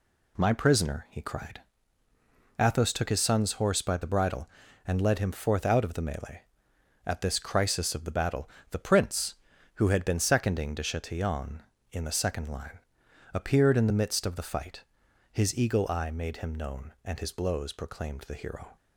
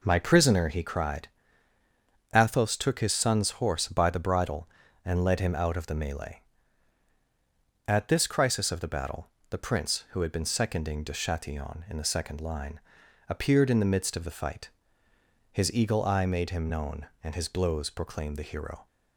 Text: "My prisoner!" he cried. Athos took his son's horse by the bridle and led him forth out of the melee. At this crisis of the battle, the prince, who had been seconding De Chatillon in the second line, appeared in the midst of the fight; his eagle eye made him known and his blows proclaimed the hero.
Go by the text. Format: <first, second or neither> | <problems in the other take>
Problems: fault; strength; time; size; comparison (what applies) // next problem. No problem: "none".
first | skips "forth"; at 5.5 s